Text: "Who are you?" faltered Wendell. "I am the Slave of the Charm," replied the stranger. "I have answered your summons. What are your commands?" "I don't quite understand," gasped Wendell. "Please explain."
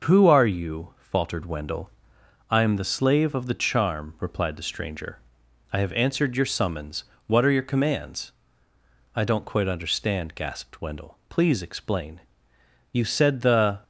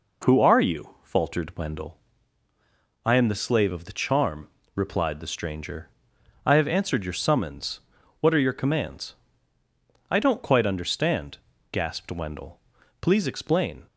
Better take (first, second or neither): second